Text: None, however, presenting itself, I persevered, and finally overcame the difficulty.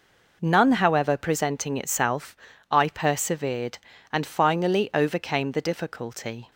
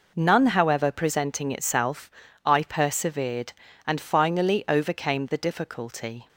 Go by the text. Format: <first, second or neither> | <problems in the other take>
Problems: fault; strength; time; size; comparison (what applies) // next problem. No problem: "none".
neither | none